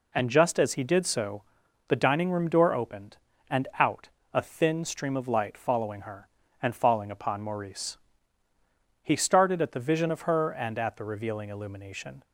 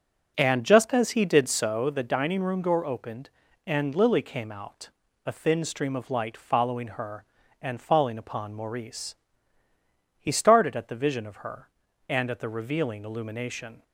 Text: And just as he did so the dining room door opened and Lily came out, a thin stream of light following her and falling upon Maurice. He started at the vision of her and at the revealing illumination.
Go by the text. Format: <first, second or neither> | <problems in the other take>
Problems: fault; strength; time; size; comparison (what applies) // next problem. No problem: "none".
second | pauses between "so" and "the"; noticeable; at 1.4 s; 0.46 s long // skips "Lily came"; at 3.7 s